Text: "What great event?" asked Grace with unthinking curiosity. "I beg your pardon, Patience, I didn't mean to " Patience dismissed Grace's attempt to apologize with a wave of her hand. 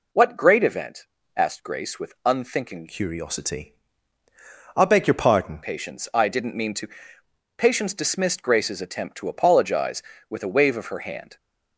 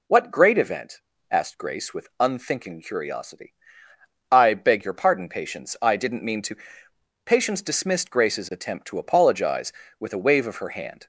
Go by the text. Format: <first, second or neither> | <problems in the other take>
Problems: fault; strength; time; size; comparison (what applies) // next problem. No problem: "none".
second | changes voice from "curiosity" to "pardon"; from 2.8 to 5.6 s; 2.8 s long